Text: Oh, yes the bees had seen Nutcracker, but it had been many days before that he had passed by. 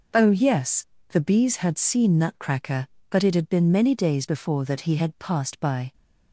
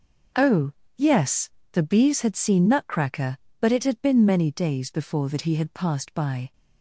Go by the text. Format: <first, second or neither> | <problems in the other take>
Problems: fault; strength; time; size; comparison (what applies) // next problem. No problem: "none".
neither | pauses between "yes" and "the"; slight; the same in both